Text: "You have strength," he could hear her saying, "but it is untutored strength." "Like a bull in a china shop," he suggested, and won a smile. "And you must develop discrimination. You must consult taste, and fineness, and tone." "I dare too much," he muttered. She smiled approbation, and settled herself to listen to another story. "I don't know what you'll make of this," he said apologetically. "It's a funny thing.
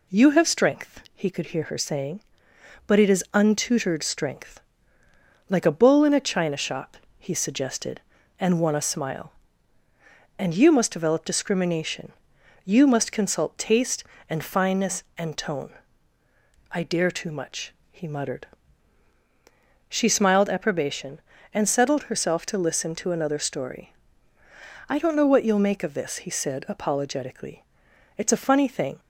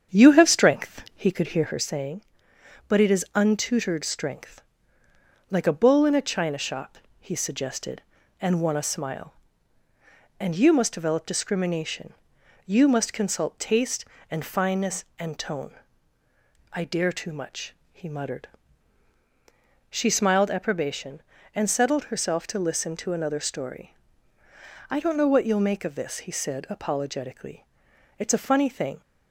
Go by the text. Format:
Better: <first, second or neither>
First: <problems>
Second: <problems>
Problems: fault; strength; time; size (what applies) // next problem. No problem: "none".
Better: first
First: none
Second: starts louder than the rest; strong; until 1.9 s; 8 dB